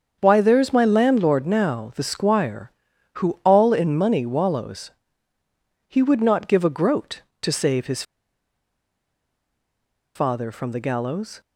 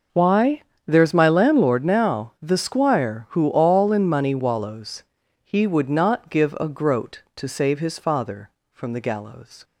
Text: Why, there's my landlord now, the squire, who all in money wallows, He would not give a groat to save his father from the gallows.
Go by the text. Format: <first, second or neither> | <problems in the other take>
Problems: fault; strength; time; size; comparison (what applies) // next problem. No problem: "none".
second | starts louder than the rest; until 1.2 s; 7 dB // pauses between "his" and "father"; strong; at 8.0 s; 2.1 s long